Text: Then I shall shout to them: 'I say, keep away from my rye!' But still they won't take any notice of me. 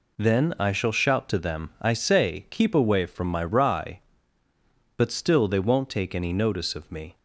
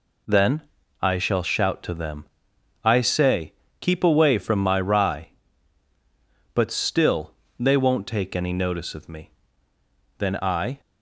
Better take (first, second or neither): first